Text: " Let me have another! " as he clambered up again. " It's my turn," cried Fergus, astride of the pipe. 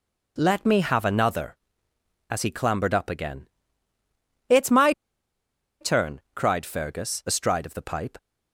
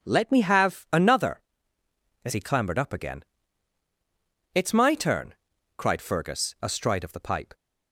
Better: second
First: pauses between "my" and "turn"; noticeable; at 4.9 s; 0.87 s long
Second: none

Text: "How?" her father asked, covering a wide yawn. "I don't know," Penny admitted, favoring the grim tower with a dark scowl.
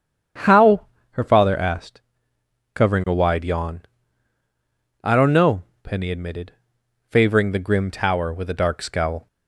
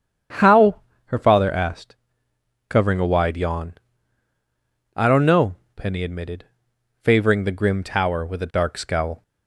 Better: neither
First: starts louder than the rest; strong; until 1.6 s; 8.5 dB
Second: starts louder than the rest; strong; until 1.6 s; 8.5 dB

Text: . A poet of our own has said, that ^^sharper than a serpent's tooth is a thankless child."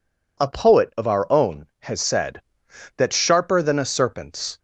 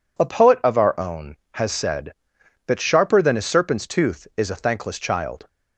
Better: second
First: stops before "tooth is a thankless child"; at 4.5 s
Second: none

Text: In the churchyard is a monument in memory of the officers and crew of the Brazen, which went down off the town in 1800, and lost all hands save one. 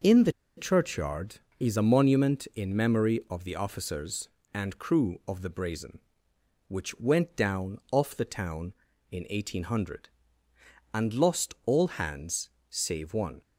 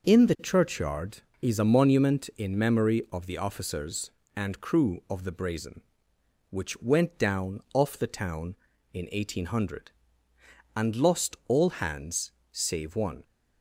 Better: second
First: pauses between "the" and "churchyard"; slight; at 0.3 s; 0.24 s long // pauses between "hands" and "save"; slight; at 12.4 s; 0.20 s long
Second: pauses between "hands" and "save"; slight; at 12.3 s; 0.20 s long

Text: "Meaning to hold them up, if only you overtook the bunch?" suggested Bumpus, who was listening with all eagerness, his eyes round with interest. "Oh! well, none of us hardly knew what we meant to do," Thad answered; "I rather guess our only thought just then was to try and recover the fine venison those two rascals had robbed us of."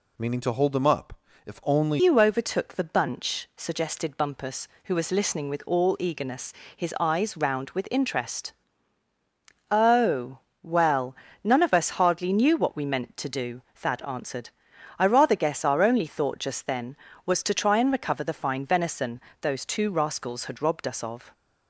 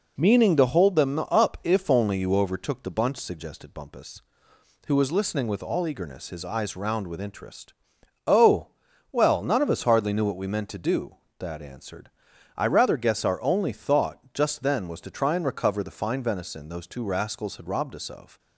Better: second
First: changes voice at "you"; from 1.9 s on; 19.4 s long // pauses between "venison" and "those"; slight; at 19.2 s; 0.20 s long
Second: none

